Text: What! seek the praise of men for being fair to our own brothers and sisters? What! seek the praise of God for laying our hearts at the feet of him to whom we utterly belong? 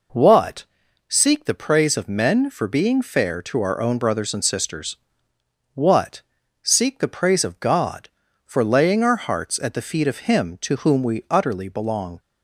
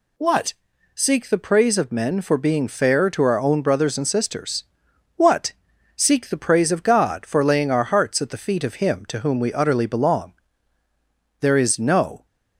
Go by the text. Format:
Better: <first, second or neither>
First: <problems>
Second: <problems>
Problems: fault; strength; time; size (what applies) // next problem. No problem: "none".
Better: first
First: none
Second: goes on to say "There is no"; noticeable; from 11.4 s on; 0.84 s long